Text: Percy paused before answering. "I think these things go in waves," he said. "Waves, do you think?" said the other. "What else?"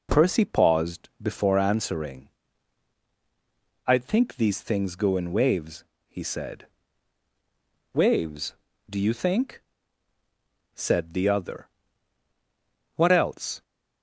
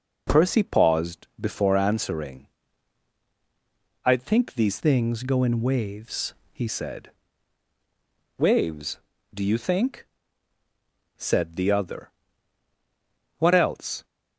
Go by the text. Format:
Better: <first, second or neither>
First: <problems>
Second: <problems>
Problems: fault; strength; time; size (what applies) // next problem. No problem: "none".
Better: first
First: none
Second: changes voice from "things" to "he"; from 4.7 to 6.6 s; 1.9 s long